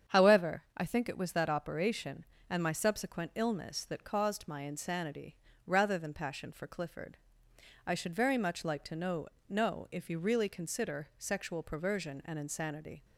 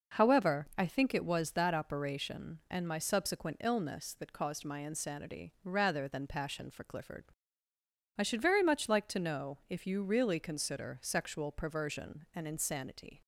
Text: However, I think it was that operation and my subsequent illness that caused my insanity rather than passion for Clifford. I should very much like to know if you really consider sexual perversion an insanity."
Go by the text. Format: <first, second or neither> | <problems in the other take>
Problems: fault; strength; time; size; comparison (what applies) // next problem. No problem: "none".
second | starts louder than the rest; strong; until 1.2 s; 8 dB // pauses between "insanity" and "rather"; slight; at 5.3 s; 0.32 s long // says "know" twice; at 9.4 s